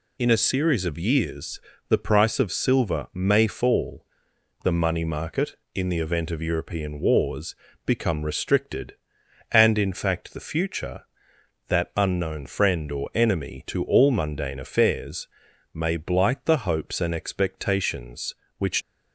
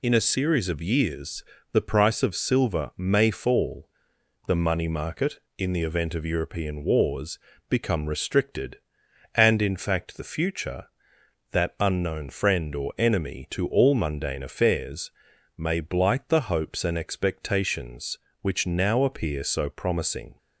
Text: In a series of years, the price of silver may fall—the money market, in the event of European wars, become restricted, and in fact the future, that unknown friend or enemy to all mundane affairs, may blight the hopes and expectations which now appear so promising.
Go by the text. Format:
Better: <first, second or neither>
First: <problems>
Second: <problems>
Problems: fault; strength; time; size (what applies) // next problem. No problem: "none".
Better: second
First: stops before "now appear so promising"; at 18.8 s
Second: none